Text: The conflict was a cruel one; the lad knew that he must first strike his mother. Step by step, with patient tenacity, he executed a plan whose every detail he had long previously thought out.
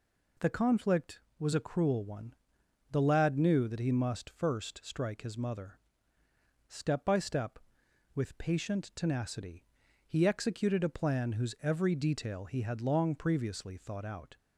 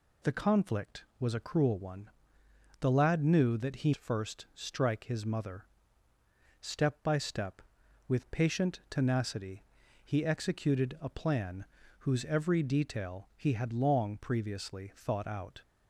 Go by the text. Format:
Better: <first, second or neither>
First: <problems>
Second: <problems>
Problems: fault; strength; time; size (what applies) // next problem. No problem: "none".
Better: first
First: none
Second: skips "must"; at 3.9 s // pauses between "plan" and "whose"; slight; at 11.6 s; 0.34 s long